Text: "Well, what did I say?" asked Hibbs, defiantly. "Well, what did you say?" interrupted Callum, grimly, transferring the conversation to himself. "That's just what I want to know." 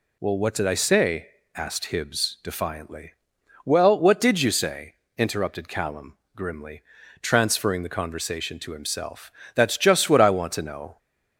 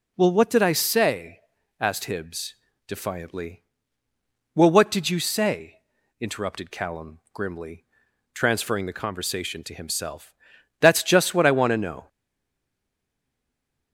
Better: first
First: none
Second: stays silent after the last word; noticeable; from 12.0 s on; 1.9 s long

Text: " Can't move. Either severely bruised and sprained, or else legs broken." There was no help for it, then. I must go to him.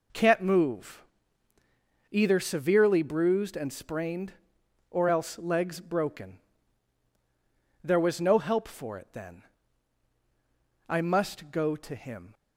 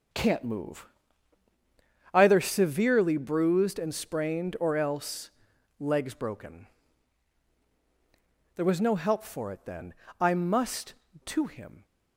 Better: first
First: none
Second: starts louder than the rest; until 2.3 s; 6.5 dB // pauses between "else" and "legs"; noticeable; at 5.2 s; 0.50 s long // skips "go"; at 11.0 s

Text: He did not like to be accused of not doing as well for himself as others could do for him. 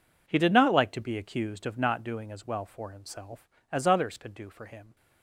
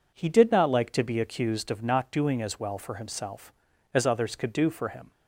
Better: neither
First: none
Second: none

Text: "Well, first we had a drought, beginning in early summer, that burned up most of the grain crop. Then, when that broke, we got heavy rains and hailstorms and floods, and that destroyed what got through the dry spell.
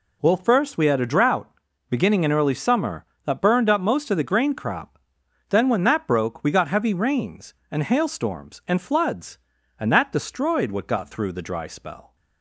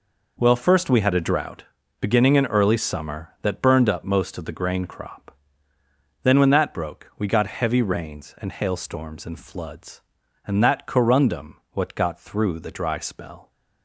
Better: first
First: none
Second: says "corundum" for "destroyed"; at 10.8 s

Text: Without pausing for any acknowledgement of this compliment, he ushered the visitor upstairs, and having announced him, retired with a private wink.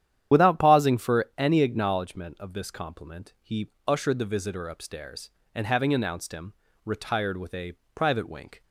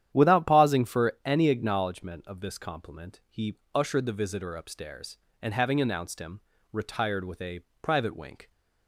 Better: second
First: loses the start of "Without"; at 0.3 s; 45 ms // starts louder than the rest; strong; until 1.4 s; 10 dB // pauses between "he" and "ushered"; slight; at 3.6 s; 0.18 s long // pauses between "a" and "private"; slight; at 7.7 s; 0.20 s long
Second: starts louder than the rest; strong; until 1.1 s; 10 dB // pauses between "he" and "ushered"; slight; at 3.5 s; 0.18 s long // pauses between "a" and "private"; slight; at 7.6 s; 0.20 s long

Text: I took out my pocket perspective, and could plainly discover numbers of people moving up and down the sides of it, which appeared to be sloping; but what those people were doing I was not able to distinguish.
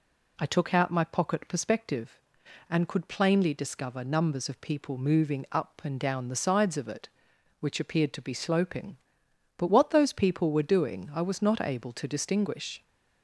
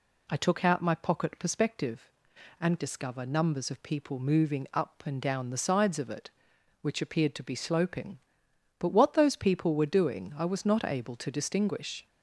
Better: first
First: none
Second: skips "could plainly"; at 2.7 s

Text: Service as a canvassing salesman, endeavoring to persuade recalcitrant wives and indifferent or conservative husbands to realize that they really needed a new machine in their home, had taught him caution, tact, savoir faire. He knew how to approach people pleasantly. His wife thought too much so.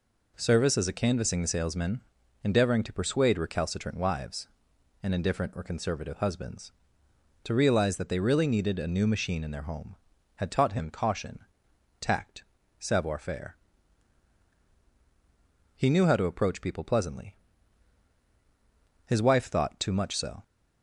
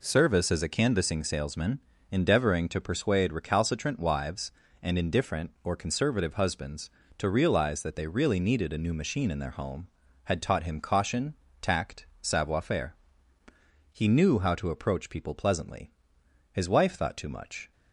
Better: first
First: none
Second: stops before "so"; at 17.7 s

